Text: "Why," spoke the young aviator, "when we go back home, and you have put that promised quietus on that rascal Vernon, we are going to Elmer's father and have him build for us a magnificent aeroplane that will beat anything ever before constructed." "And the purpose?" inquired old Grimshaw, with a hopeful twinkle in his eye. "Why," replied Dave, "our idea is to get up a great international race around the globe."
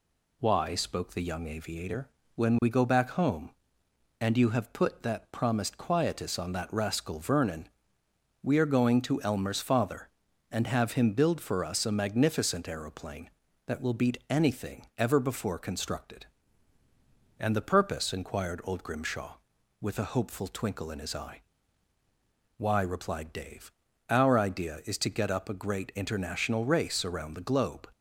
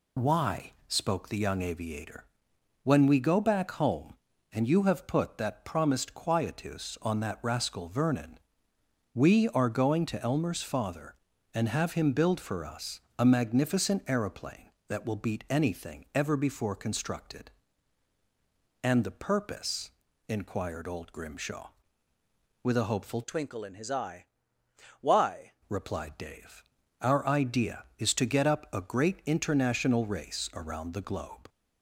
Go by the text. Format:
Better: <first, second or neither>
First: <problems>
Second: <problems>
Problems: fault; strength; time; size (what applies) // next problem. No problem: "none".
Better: first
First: none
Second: pauses between "us" and "a"; slight; at 12.9 s; 0.20 s long // changes voice from "twinkle" to "Why"; from 23.2 to 25.5 s; 2.3 s long